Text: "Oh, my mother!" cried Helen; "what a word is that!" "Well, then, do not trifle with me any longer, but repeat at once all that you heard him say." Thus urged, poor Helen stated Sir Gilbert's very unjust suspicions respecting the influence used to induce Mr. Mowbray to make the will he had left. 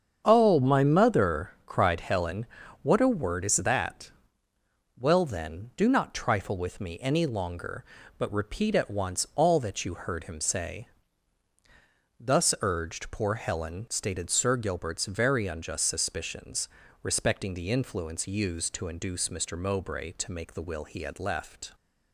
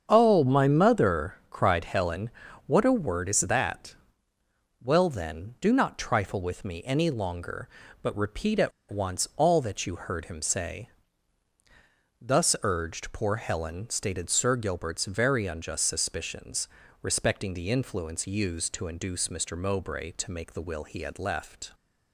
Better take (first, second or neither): first